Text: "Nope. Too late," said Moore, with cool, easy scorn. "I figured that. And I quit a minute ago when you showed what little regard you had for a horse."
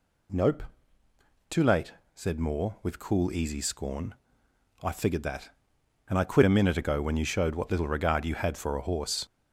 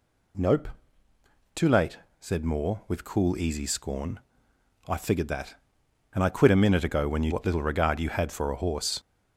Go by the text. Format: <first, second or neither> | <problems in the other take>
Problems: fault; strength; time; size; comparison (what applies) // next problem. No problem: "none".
first | skips "showed"; at 7.3 s